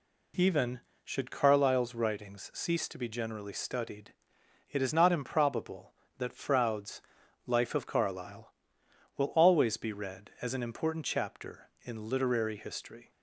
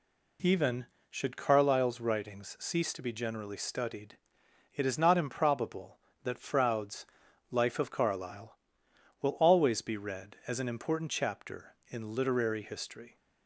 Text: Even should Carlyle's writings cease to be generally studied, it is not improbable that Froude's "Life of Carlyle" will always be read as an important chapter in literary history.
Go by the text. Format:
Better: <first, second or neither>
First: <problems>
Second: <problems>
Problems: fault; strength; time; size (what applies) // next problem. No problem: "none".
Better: neither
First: pauses between "Froude's" and "Life"; at 7.0 s; 0.44 s long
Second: pauses between "Froude's" and "Life"; at 7.0 s; 0.44 s long